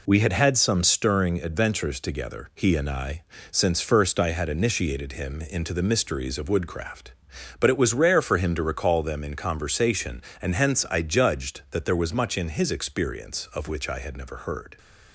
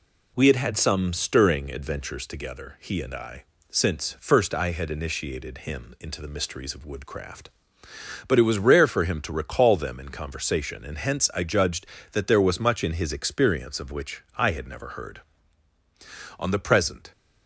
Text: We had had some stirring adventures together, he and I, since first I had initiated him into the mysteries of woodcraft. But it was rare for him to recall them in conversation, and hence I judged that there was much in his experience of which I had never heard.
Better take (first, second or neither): first